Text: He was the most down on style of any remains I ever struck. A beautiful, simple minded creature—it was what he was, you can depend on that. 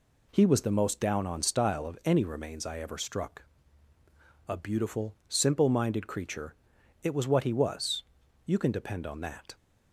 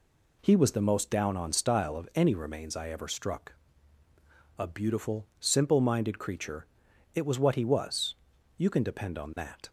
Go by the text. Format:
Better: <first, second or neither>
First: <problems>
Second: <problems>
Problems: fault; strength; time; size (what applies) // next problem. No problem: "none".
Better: neither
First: none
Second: none